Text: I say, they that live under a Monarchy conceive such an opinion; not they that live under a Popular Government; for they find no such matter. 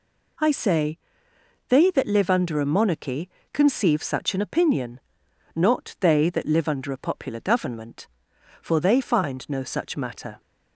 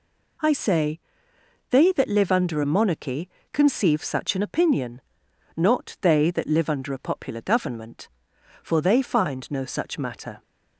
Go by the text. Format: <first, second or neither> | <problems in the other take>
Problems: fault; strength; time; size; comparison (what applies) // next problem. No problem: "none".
neither | pauses between "Monarchy" and "conceive"; slight; the same in both